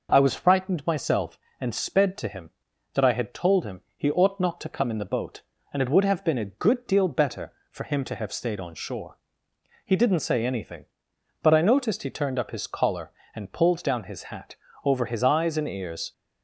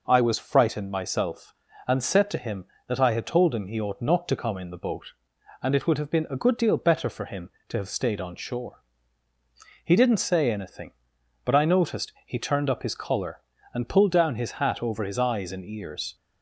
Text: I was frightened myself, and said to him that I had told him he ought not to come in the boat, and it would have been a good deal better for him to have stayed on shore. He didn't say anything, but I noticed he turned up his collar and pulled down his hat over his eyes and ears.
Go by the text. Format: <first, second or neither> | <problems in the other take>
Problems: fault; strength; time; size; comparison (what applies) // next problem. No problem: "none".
second | says "sped" for "said"; at 1.7 s // pauses between "him" and "he"; slight; at 3.8 s; 0.16 s long // pauses between "hat" and "over"; slight; at 14.5 s; 0.28 s long